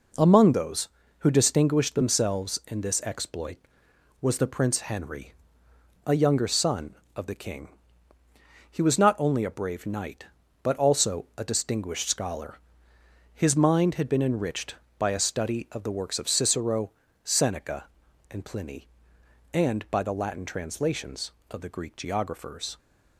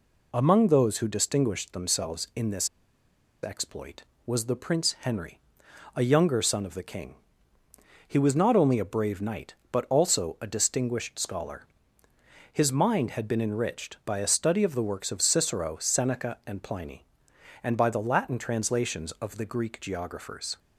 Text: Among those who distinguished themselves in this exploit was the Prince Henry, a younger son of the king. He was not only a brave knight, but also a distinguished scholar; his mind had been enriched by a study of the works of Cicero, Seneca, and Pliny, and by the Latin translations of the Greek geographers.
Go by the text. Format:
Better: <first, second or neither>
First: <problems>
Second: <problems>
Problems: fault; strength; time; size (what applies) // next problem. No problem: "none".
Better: first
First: none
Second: pauses between "this" and "exploit"; noticeable; at 2.6 s; 0.75 s long